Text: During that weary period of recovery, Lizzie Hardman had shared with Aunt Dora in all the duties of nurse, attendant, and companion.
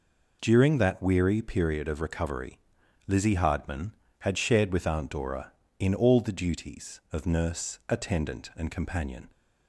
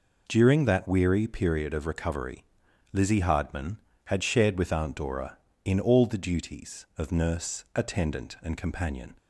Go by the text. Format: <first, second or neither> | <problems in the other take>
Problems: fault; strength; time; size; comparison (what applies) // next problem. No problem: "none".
neither | none